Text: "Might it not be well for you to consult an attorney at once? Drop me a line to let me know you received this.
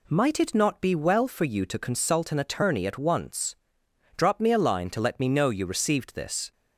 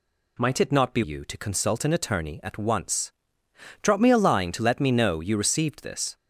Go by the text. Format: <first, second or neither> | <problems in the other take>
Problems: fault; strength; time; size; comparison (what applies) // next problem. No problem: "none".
first | skips "well for"; at 1.0 s